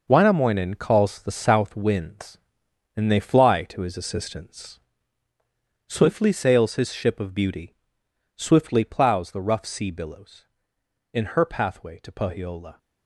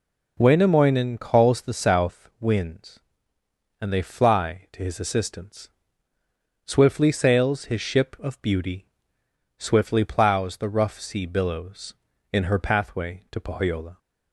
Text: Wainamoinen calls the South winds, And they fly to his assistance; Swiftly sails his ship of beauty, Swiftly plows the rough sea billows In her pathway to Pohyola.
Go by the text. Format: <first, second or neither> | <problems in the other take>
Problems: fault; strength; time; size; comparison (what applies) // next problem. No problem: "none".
second | gets quieter; strong; throughout; 9.5 dB